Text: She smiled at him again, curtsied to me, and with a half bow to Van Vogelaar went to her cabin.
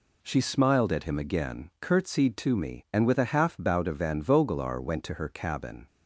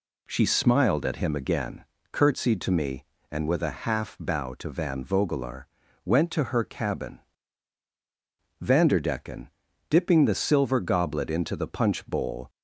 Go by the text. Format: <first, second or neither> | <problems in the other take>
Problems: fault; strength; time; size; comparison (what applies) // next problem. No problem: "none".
first | pauses between "Vogelaar" and "went"; at 5.6 s; 0.38 s long // goes on to say "Vanderdecken dipping the silver goblet into the punch bowl"; strong; from 8.6 s on; 3.8 s long